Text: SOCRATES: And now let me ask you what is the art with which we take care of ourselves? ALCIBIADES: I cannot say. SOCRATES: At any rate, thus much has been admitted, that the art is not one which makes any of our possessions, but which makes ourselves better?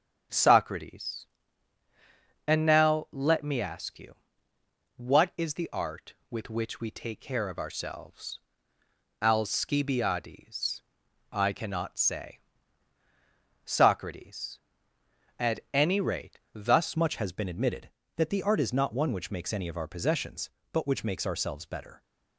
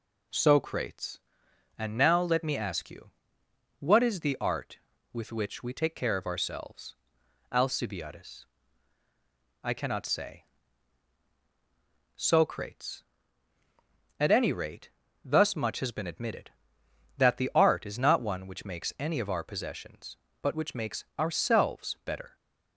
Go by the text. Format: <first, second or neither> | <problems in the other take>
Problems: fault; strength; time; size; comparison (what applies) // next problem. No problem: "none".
second | starts louder than the rest; strong; until 2.5 s; 7.5 dB // pauses between "you" and "what"; noticeable; at 4.1 s; 0.80 s long; noticeable in the second // changes voice at "much"; from 16.9 s on; 5.1 s long